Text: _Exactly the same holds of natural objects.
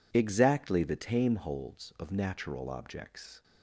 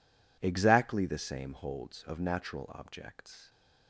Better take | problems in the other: second | says "tame" for "same"; at 0.9 s

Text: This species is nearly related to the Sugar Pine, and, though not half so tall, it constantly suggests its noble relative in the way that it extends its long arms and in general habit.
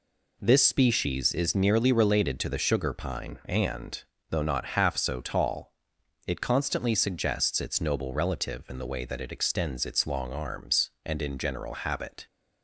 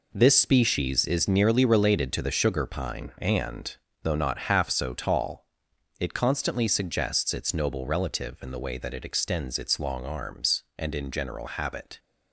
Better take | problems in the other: first | gets quieter; strong; throughout; 9 dB

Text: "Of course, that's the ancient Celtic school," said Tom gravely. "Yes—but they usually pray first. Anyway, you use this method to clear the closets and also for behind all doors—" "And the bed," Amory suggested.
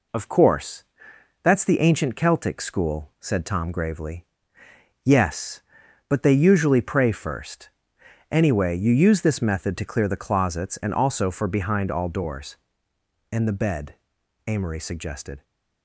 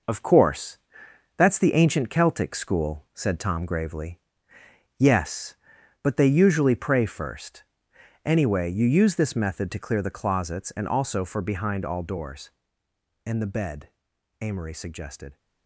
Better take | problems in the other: first | gets quieter; noticeable; throughout; 6 dB

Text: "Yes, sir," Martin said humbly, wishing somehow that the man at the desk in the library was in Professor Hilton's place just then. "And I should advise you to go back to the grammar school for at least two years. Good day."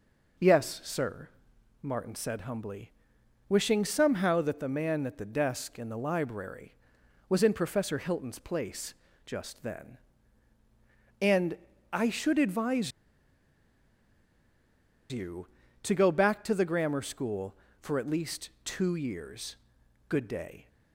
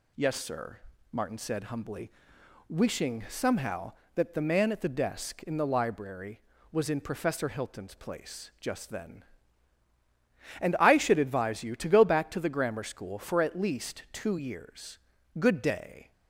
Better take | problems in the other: second | pauses between "place" and "just"; slight; at 8.9 s; 0.32 s long // pauses between "And" and "I"; slight; at 11.5 s; 0.34 s long // pauses between "advise" and "you"; strong; at 12.9 s; 2.2 s long // pauses between "least" and "two"; slight; at 18.4 s; 0.16 s long

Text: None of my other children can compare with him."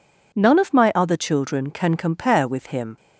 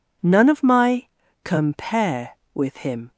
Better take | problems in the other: first | skips "other children can"; at 1.2 s

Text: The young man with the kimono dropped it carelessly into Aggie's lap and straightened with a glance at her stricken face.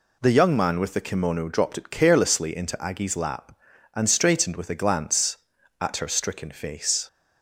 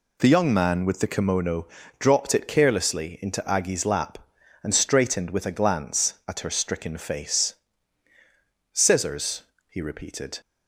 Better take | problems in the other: first | pauses between "kimono" and "dropped"; slight; at 1.6 s; 0.32 s long // goes on to say "Scissors he repeated"; from 8.7 s on; 1.6 s long

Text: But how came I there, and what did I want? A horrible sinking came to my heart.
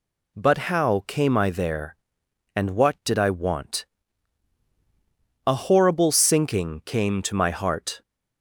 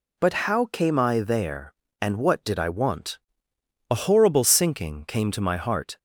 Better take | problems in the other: first | gets quieter; noticeable; throughout; 5.5 dB

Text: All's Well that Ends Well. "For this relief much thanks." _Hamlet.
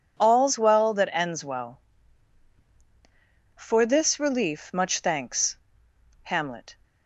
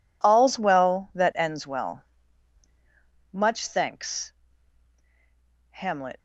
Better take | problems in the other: first | skips "For this relief"; at 2.6 s

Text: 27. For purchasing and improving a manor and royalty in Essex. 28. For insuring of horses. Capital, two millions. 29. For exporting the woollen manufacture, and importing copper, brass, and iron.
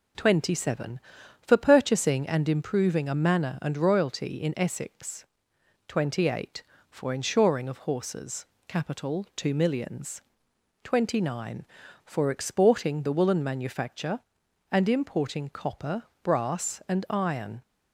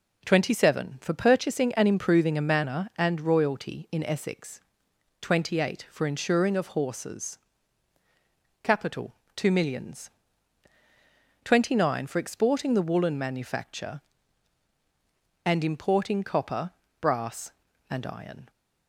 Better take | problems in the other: neither | none

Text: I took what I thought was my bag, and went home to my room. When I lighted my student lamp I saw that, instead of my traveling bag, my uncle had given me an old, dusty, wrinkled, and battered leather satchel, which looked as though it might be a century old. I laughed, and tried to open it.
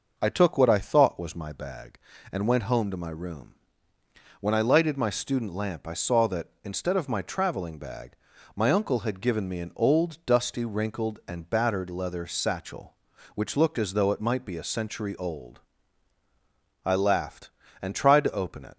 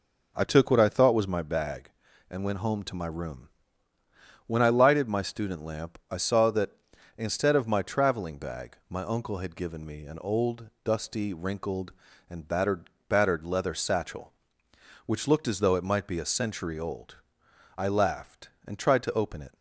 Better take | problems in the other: first | says "battered" twice; at 13.0 s

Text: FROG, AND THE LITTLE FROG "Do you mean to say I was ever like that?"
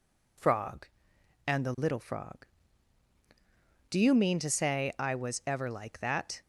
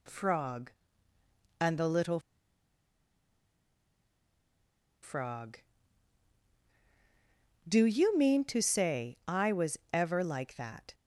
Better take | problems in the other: first | pauses between "LITTLE" and "FROG"; strong; at 2.2 s; 2.8 s long

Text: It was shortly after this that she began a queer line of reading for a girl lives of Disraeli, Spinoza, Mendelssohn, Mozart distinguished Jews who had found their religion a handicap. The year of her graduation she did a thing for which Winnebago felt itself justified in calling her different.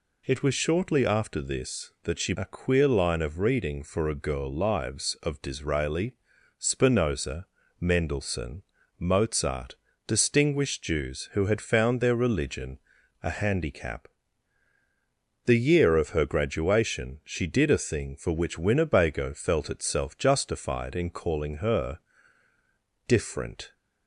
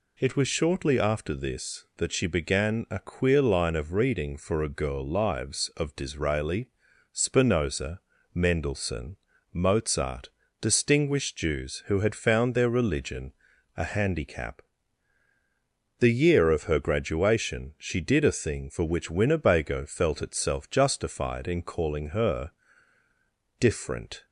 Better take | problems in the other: second | skips "began"; at 2.3 s // pauses between "Mozart" and "distinguished"; slight; at 9.7 s; 0.32 s long; slight in the second // pauses between "religion" and "a"; at 12.7 s; 0.44 s long; also in the second // pauses between "her" and "different"; at 21.9 s; 1.0 s long; also in the second

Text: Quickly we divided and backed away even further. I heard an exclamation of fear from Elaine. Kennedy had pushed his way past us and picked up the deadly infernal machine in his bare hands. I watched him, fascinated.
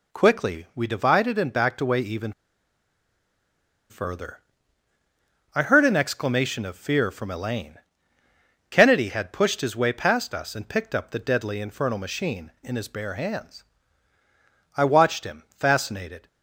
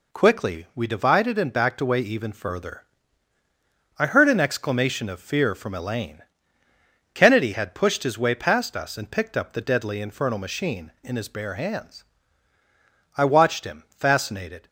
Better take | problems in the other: second | pauses between "even" and "further"; strong; at 2.3 s; 1.5 s long

